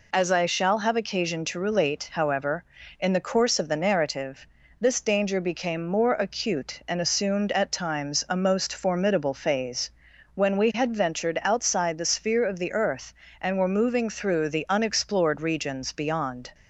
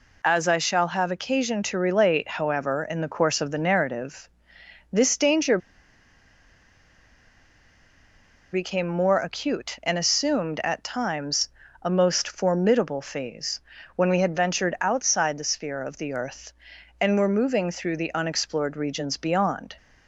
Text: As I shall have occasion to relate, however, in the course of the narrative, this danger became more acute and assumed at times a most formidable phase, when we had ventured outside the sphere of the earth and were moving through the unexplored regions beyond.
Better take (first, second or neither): first